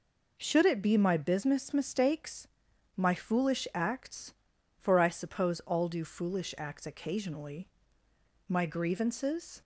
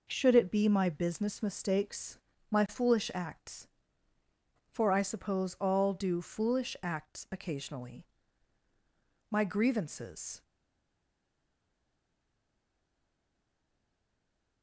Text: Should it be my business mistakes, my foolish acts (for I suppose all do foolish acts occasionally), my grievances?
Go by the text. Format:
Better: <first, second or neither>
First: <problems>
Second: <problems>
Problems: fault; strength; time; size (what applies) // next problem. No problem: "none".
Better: first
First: none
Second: stays silent after the last word; strong; from 10.4 s on; 4.2 s long